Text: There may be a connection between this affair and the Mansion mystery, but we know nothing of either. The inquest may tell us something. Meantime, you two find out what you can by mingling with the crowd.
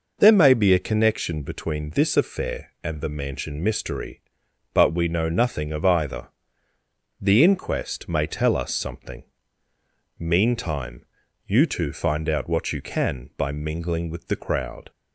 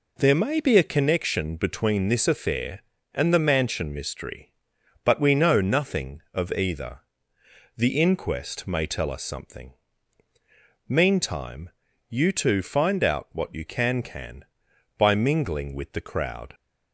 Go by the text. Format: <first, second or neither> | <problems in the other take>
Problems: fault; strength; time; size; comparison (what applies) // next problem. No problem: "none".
first | says "can" twice; at 14.0 s